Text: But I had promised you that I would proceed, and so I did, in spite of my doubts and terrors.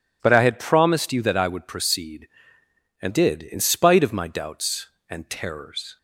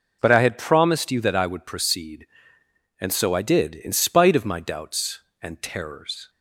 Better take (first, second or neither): second